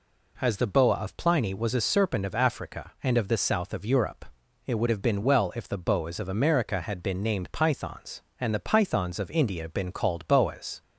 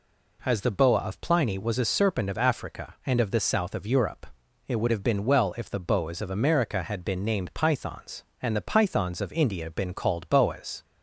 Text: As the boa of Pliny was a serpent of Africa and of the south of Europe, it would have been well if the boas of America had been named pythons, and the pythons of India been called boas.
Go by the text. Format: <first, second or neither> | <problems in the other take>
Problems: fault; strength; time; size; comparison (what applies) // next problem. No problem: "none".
neither | none